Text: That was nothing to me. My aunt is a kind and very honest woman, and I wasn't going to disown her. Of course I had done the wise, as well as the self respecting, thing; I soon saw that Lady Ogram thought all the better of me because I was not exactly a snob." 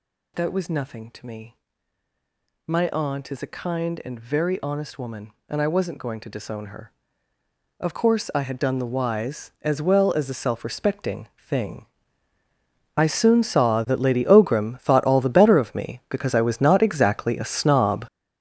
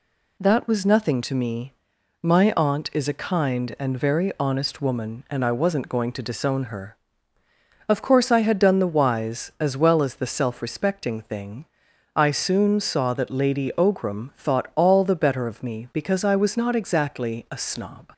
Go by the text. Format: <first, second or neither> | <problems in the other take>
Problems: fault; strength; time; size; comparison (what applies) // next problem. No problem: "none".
second | gets louder; strong; throughout; 10 dB